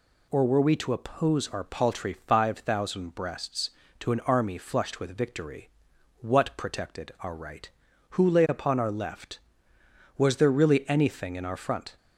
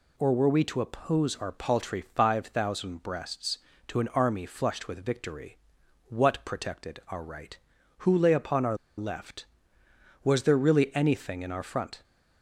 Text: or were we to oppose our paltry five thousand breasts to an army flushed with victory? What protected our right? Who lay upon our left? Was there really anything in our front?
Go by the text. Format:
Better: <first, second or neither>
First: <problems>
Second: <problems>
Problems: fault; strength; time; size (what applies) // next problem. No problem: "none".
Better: first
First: none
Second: pauses between "our" and "left"; slight; at 8.7 s; 0.21 s long